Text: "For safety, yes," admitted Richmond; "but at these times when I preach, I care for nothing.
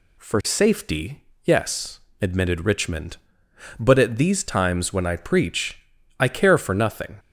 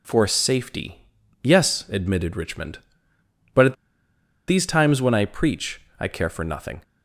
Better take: first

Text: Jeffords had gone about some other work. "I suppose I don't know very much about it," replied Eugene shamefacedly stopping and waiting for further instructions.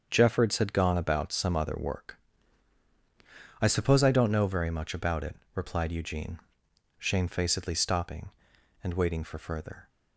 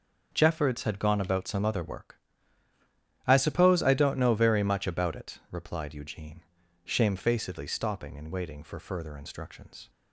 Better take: second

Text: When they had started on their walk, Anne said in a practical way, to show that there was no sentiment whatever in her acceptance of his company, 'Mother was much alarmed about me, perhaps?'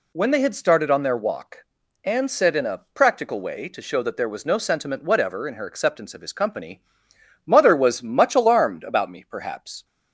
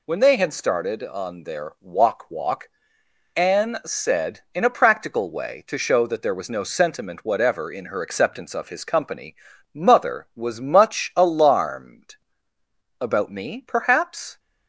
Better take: first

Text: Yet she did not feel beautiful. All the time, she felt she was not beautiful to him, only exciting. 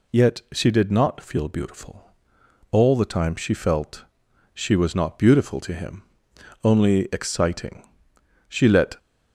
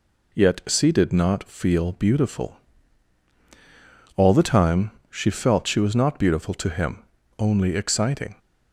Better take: second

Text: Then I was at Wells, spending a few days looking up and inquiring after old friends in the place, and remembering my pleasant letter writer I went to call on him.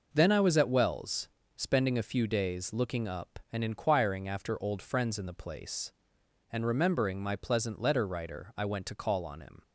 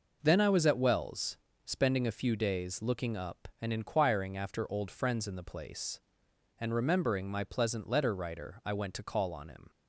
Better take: neither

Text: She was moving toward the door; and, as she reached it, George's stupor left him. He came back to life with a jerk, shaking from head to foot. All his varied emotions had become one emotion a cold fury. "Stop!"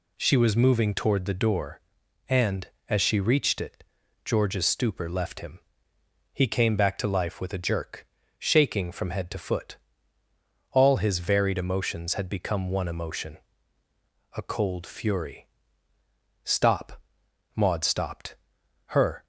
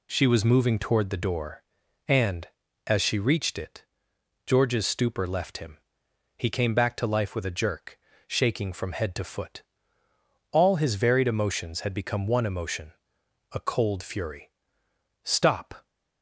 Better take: second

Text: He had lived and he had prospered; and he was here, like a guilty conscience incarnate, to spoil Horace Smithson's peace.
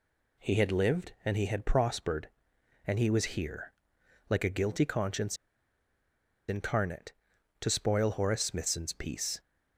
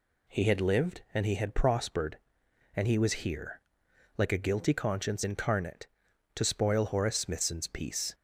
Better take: second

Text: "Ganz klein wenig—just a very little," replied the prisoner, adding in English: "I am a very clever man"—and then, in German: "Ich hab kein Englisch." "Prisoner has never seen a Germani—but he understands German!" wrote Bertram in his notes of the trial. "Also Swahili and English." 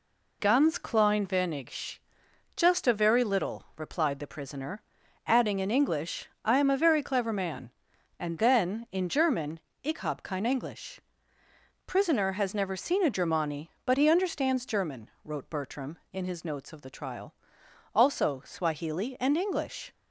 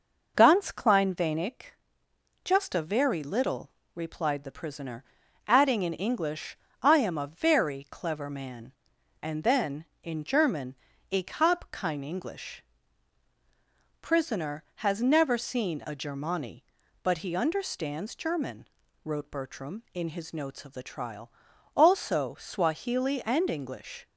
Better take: neither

